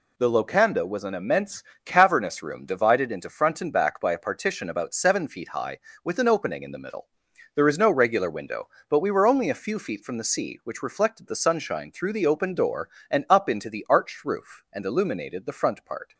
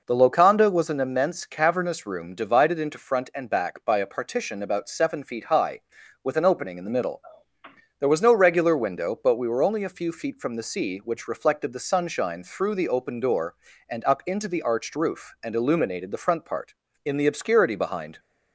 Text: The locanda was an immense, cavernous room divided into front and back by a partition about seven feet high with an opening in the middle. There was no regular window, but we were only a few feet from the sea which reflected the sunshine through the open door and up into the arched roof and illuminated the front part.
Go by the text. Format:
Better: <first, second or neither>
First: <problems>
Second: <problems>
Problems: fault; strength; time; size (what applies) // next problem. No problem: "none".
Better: first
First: none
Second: goes on to say "In the obscurity behind"; noticeable; from 17.0 s on; 1.1 s long